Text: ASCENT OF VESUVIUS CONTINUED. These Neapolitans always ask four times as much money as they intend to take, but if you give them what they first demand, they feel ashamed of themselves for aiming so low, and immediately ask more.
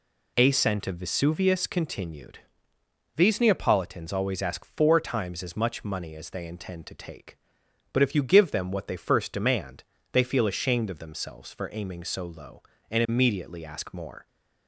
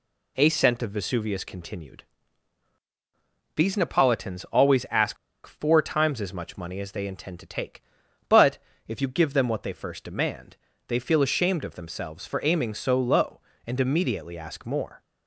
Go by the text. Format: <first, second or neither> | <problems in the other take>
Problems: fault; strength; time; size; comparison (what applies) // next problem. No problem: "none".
first | pauses between "ask" and "four"; slight; at 5.1 s; 0.30 s long // pauses between "but" and "if"; slight; at 8.5 s; 0.28 s long